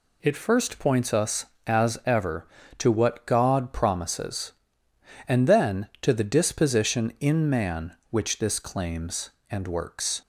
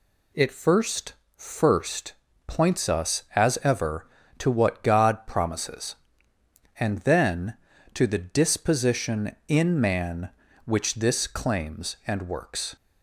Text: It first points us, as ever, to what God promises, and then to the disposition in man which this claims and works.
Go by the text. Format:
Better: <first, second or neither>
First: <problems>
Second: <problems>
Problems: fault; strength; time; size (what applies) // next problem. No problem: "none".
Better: first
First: none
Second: says "first" twice; at 1.3 s